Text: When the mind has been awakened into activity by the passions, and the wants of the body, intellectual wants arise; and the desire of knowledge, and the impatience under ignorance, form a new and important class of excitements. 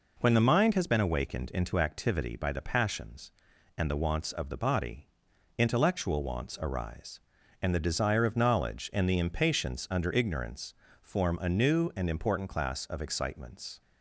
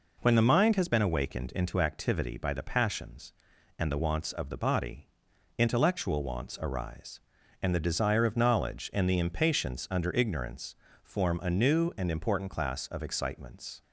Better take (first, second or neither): neither